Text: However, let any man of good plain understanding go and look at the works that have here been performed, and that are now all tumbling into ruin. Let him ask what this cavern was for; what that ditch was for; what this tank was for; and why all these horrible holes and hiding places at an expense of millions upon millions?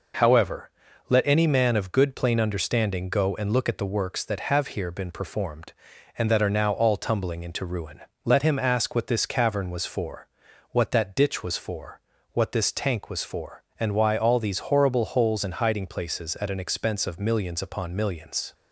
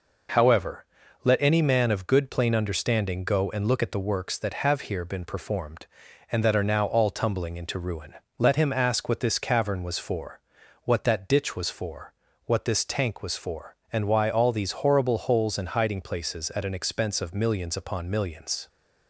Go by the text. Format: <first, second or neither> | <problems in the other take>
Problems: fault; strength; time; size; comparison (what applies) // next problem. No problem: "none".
neither | none